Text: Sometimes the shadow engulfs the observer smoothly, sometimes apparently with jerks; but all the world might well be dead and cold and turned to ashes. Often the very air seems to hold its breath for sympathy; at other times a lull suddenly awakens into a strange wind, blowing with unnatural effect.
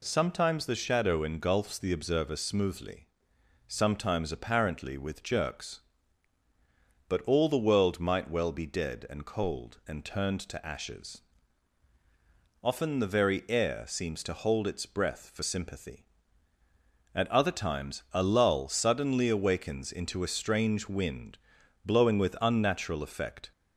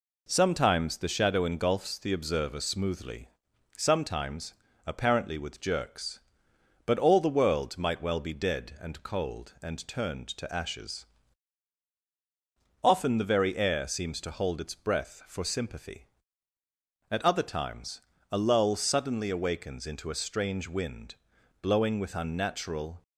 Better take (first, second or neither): first